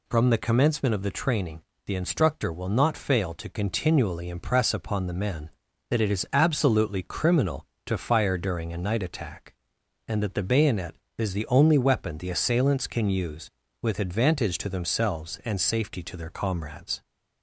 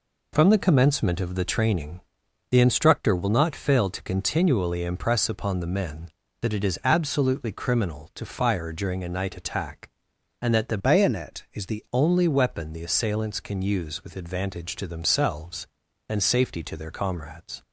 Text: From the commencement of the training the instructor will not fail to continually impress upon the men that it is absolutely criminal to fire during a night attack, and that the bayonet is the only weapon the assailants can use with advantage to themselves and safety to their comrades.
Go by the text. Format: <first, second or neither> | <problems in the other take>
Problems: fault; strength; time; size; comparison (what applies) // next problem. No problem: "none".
first | pauses between "training" and "the"; noticeable; at 1.9 s; 0.50 s long; slight in the first // changes voice from "bayonet" to "the"; from 10.7 to 11.8 s; 1.1 s long